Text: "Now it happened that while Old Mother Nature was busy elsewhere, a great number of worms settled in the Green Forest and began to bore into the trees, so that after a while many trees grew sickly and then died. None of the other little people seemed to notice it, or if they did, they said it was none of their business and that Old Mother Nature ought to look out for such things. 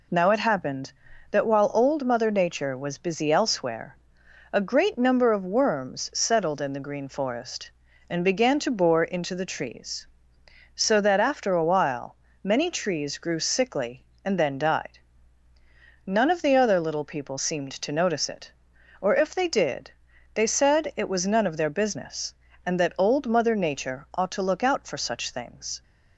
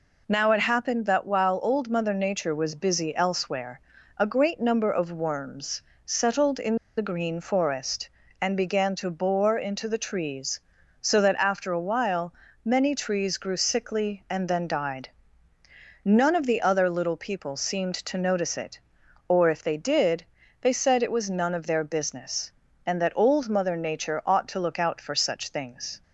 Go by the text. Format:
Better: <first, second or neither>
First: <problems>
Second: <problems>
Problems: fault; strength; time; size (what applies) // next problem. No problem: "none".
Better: first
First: pauses between "while" and "many"; slight; at 12.1 s; 0.26 s long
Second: pauses between "worms" and "settled"; slight; at 5.8 s; 0.24 s long // pauses between "in" and "the"; slight; at 6.7 s; 0.21 s long // pauses between "while" and "many"; slight; at 12.3 s; 0.28 s long